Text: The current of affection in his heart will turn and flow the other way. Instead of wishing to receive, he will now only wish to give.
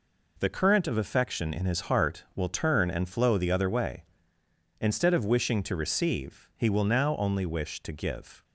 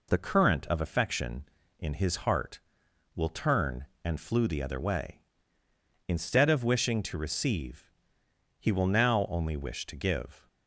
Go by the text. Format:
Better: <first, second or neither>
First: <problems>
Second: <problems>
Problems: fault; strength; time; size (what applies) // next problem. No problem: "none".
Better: first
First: none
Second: says "flew" for "flow"; at 4.1 s